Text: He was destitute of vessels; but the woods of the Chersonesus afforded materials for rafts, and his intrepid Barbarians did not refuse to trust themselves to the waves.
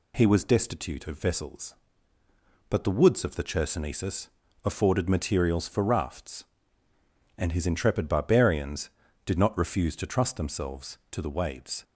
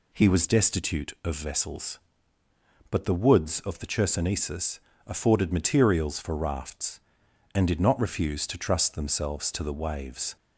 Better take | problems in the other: first | pauses between "Chersonesus" and "afforded"; slight; at 4.7 s; 0.28 s long; slight in the first // skips "his intrepid Barbarians"; at 7.6 s

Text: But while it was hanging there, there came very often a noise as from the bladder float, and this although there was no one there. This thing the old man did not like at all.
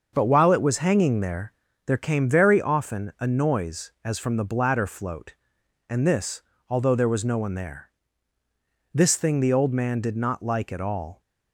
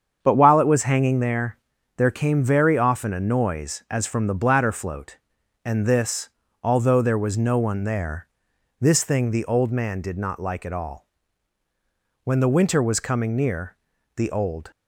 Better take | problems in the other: first | starts louder than the rest; strong; until 1.2 s; 7.5 dB; also in the first // pauses between "this" and "although"; slight; at 6.2 s; 0.34 s long; slight in the first // goes on to say "When the winter was coming near the old"; strong; from 12.2 s on; 2.4 s long

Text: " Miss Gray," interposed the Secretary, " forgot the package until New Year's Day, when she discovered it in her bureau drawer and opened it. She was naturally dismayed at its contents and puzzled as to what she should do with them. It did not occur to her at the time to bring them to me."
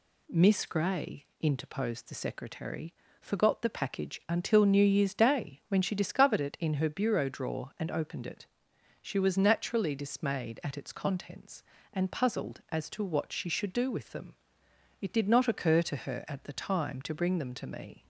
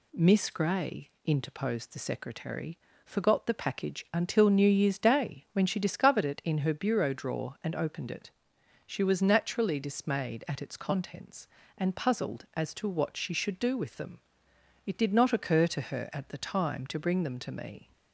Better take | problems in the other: neither | none

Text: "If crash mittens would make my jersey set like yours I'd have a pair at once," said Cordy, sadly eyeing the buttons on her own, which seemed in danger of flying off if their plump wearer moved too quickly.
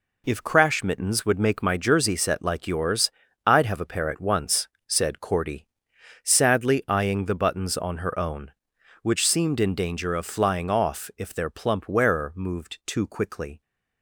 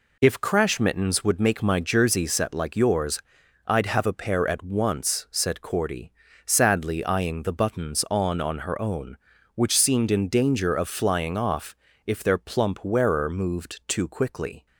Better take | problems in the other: first | pauses between "yours" and "I'd"; noticeable; at 3.1 s; 0.48 s long; slight in the first // says "on" twice; at 8.3 s // pauses between "off" and "if"; slight; at 11.7 s; 0.28 s long

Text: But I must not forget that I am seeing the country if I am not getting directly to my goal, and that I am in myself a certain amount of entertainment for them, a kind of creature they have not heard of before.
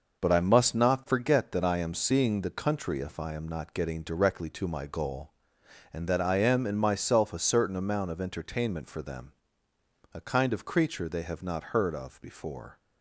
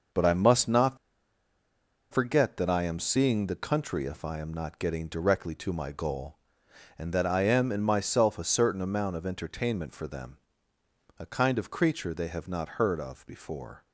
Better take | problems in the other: first | pauses between "not" and "forget"; at 0.9 s; 1.1 s long

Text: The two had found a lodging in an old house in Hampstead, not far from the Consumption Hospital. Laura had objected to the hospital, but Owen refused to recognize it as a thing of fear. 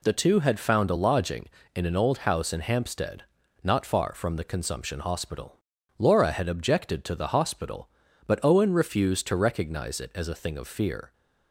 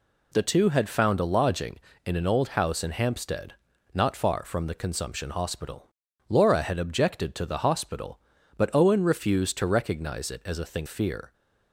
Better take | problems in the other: first | skips "of"; at 10.8 s

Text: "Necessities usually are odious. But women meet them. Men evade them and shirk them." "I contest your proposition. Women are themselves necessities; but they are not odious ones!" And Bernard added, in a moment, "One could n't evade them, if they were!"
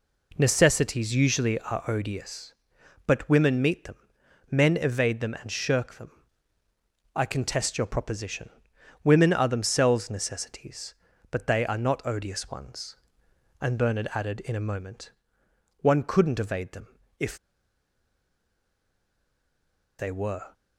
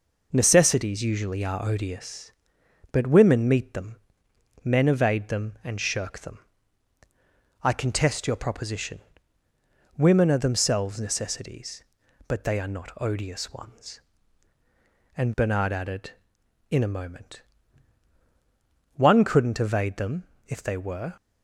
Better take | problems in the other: second | pauses between "if" and "they"; strong; at 17.3 s; 2.6 s long

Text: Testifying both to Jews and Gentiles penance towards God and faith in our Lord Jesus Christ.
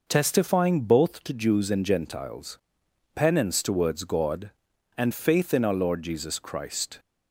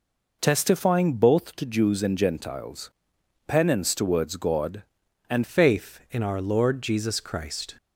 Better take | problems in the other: first | pauses between "Gentiles" and "penance"; noticeable; at 2.9 s; 0.58 s long; noticeable in the first // changes voice at "faith"; from 5.4 s on; 2.3 s long

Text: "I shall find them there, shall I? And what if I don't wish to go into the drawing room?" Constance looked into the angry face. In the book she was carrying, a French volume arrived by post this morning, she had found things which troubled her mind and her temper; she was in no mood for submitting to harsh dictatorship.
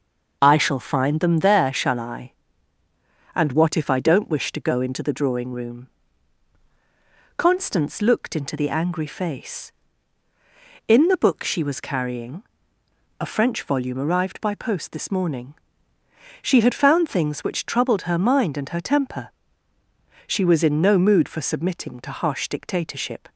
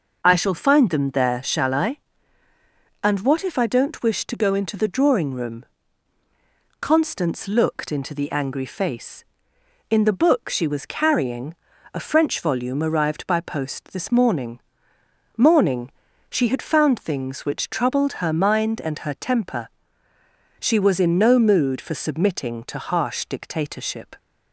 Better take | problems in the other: first | says "morning" twice; at 15.3 s

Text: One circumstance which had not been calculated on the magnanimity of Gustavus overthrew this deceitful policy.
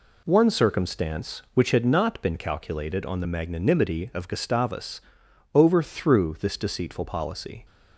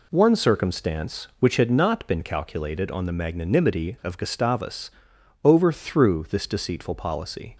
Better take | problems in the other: neither | pauses between "Gustavus" and "overthrew"; noticeable; the same in both

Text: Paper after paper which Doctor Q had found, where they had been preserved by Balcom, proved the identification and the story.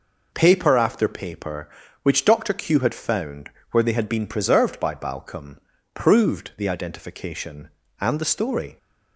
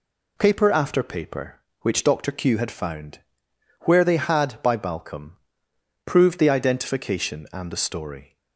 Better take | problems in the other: first | skips "been preserved"; at 4.6 s

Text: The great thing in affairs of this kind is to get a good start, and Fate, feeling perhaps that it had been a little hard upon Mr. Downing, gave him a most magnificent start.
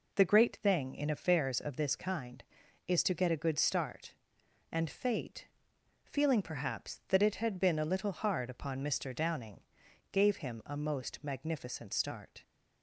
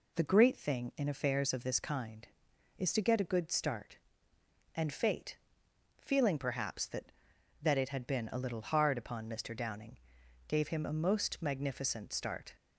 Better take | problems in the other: first | says "that" twice; at 7.6 s

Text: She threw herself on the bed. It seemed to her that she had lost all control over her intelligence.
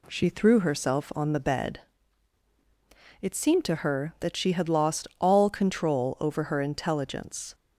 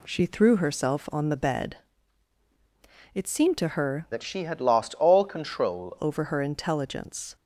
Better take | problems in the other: first | changes voice from "that" to "control"; from 4.1 to 5.9 s; 1.8 s long

